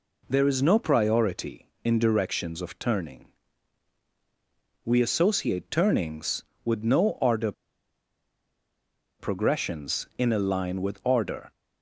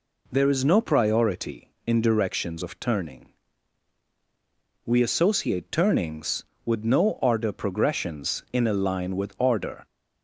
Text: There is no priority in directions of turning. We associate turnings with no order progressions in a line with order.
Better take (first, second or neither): second